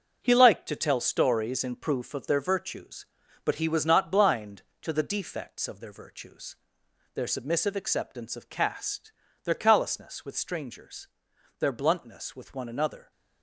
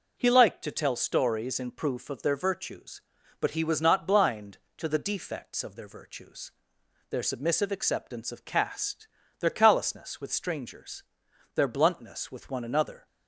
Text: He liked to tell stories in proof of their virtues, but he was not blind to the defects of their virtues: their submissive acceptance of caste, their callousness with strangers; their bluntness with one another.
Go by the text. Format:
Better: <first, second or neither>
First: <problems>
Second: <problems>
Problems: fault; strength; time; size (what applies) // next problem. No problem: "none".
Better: second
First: gets quieter; strong; throughout; 8 dB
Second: none